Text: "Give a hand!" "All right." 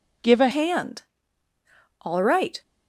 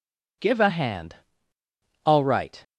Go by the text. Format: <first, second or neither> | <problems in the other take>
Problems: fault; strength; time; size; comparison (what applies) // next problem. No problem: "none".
second | changes voice at "hand"; from 0.5 s on; 2.1 s long